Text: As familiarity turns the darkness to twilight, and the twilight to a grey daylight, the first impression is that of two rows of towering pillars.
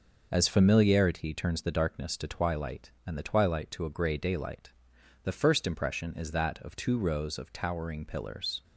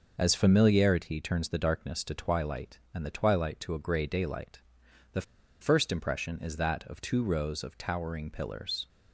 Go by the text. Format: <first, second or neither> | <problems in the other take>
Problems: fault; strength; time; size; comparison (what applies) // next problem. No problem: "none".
first | pauses between "the" and "first"; at 5.2 s; 0.38 s long